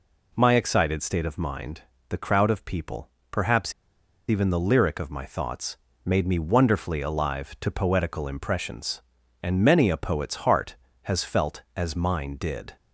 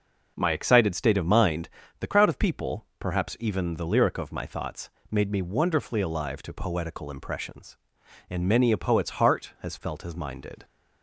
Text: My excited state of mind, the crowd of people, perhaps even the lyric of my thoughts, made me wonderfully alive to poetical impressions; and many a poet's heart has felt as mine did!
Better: second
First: pauses between "perhaps" and "even"; noticeable; at 3.7 s; 0.57 s long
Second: none

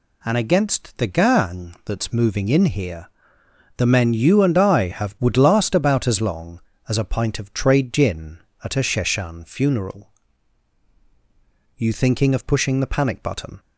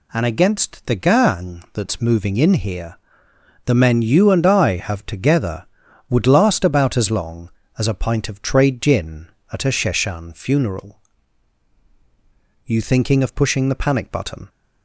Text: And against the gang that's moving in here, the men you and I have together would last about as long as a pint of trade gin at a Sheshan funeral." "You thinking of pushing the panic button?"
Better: second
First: skips "together"; at 5.1 s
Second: none

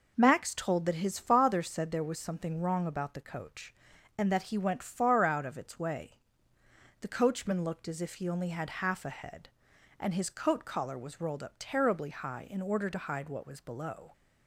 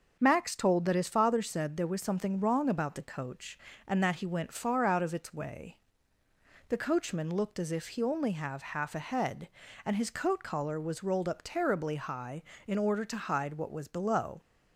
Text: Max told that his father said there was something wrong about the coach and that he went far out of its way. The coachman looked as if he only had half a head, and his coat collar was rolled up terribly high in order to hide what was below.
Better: first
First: none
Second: starts louder than the rest; until 1.2 s; 6 dB // says "have" for "had"; at 8.3 s

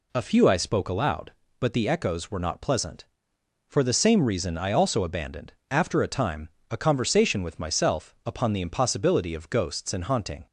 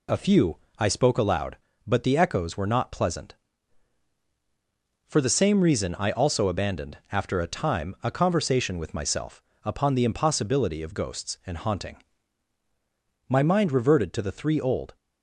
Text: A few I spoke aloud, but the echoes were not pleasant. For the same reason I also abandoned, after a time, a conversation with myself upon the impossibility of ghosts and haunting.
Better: first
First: none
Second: pauses between "few" and "I"; slight; at 0.5 s; 0.22 s long // pauses between "myself" and "upon"; slight; at 9.4 s; 0.20 s long // goes on to say "My mind reverted to the three old"; strong; from 13.2 s on; 1.6 s long

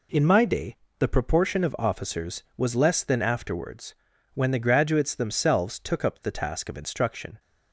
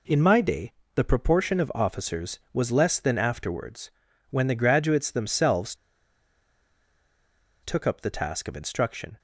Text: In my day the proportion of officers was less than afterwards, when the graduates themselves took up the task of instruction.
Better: first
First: pauses between "day" and "the"; slight; at 0.7 s; 0.24 s long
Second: pauses between "day" and "the"; slight; at 0.7 s; 0.24 s long // pauses between "themselves" and "took"; strong; at 5.7 s; 1.8 s long

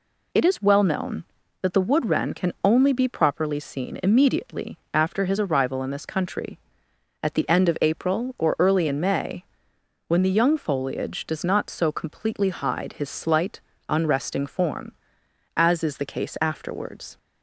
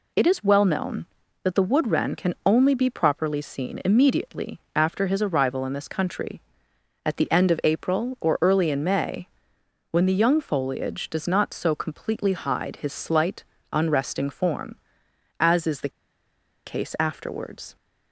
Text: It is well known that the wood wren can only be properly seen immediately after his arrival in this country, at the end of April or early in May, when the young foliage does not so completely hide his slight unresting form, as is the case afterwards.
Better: first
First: pauses between "immediately" and "after"; slight; at 4.7 s; 0.16 s long // pauses between "slight" and "unresting"; slight; at 13.5 s; 0.30 s long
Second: pauses between "immediately" and "after"; slight; at 4.5 s; 0.16 s long // pauses between "slight" and "unresting"; slight; at 13.4 s; 0.30 s long // pauses between "the" and "case"; noticeable; at 15.9 s; 0.77 s long

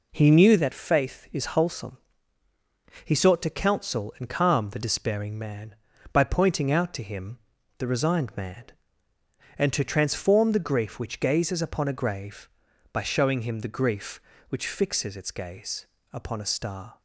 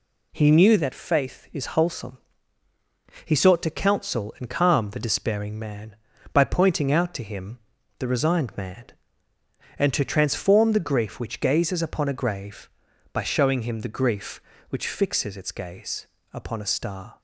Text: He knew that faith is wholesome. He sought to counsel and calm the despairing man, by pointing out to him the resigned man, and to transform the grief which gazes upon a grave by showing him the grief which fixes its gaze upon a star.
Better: second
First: starts louder than the rest; until 1.6 s; 4 dB // pauses between "him" and "the"; at 7.3 s; 0.40 s long // pauses between "gaze" and "upon"; slight; at 15.8 s; 0.26 s long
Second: pauses between "him" and "the"; at 7.5 s; 0.40 s long // pauses between "gaze" and "upon"; slight; at 16.0 s; 0.26 s long

